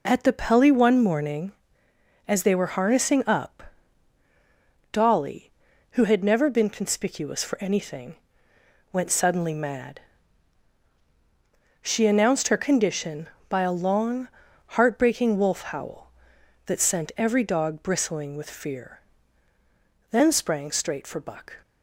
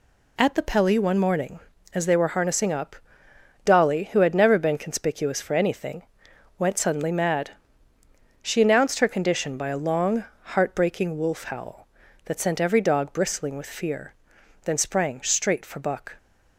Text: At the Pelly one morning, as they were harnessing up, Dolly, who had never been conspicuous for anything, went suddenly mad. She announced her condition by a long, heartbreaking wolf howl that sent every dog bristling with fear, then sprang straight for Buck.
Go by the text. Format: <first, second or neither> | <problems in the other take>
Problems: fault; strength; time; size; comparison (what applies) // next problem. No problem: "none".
neither | none